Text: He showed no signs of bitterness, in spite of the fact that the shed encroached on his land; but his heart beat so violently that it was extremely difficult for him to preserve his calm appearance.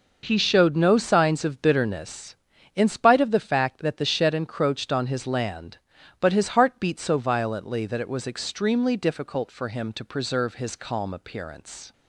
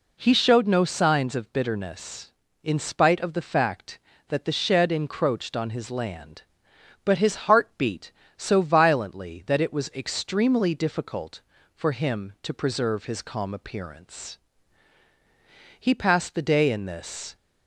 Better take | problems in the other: first | goes on to say "He passed the day in this"; from 15.7 s on; 1.5 s long

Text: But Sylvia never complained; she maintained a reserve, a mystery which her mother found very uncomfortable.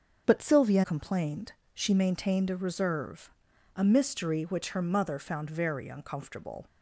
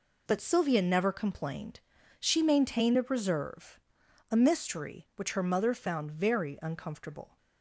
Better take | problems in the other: second | starts louder than the rest; noticeable; until 1.2 s; 6 dB // skips "never"; at 0.8 s

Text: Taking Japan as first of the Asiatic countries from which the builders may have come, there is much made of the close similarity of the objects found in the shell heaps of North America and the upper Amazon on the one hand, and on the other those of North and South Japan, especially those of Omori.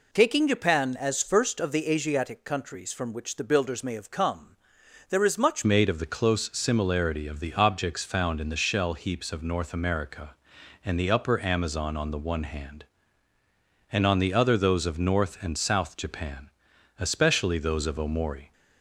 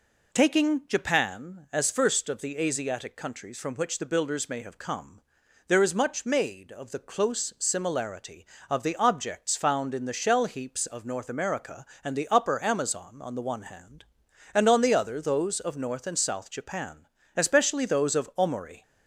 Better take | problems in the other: second | changes voice at "made"; from 5.6 s on; 12.9 s long

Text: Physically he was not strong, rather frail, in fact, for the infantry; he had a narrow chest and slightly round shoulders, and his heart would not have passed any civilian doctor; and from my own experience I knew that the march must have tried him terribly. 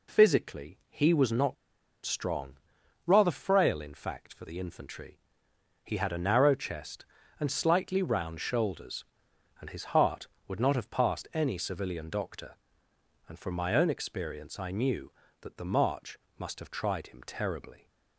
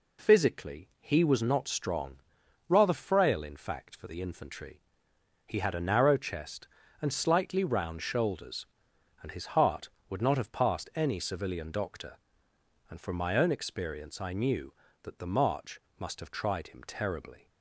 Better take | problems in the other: second | pauses between "not" and "strong"; noticeable; at 1.5 s; 0.48 s long // pauses between "march" and "must"; slight; at 16.1 s; 0.22 s long; slight in the second

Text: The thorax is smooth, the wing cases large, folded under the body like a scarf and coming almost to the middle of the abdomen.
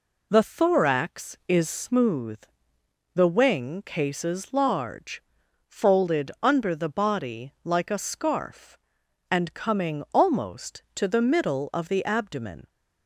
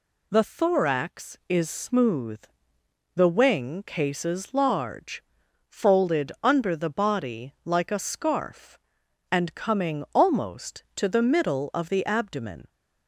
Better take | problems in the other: second | starts louder than the rest; slight; until 1.9 s; 3 dB

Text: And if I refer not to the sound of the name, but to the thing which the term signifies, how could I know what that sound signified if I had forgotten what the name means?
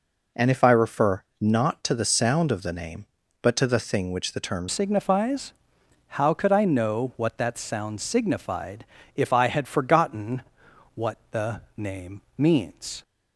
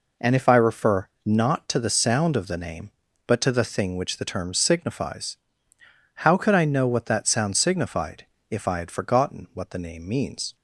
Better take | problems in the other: second | pauses between "refer" and "not"; slight; at 1.2 s; 0.16 s long; slight in the second // changes voice at "signifies"; from 4.6 s on; 8.4 s long // pauses between "signified" and "if"; slight; at 8.8 s; 0.30 s long; slight in the second // pauses between "forgotten" and "what"; noticeable; at 10.4 s; 0.52 s long // pauses between "the" and "name"; slight; at 11.5 s; 0.16 s long // pauses between "name" and "means"; slight; at 12.2 s; 0.16 s long

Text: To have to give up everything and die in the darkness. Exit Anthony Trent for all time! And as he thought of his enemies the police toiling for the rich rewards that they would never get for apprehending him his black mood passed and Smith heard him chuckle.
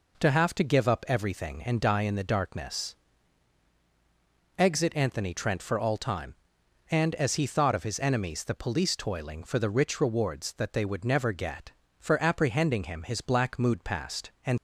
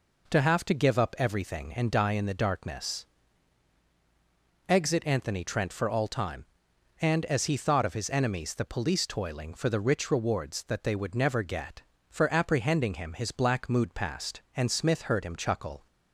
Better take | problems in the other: second | stops before "Smith heard him chuckle"; at 14.5 s

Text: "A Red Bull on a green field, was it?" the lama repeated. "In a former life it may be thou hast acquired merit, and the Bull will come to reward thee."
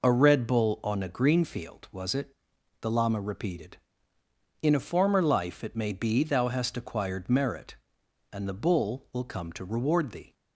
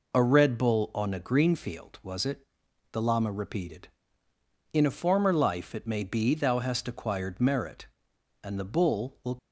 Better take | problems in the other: first | stops before "come to reward thee"; at 9.3 s

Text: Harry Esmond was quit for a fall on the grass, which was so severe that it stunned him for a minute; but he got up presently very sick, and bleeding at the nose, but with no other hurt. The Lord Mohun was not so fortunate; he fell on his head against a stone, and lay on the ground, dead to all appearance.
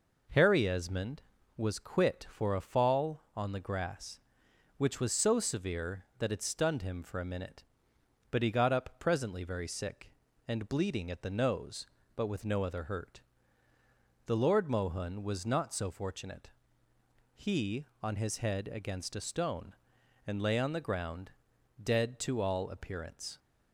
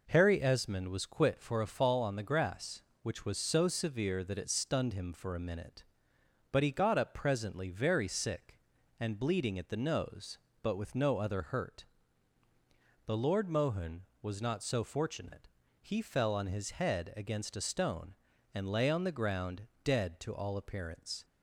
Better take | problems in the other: second | skips "fell"; at 17.9 s

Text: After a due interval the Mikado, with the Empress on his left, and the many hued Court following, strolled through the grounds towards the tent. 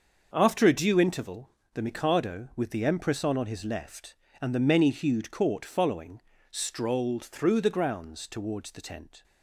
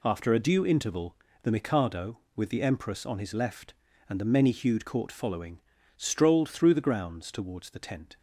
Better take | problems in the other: second | starts louder than the rest; until 1.3 s; 6.5 dB // pauses between "interval" and "the"; slight; at 1.4 s; 0.24 s long; slight in the second // says "on" twice; at 3.3 s

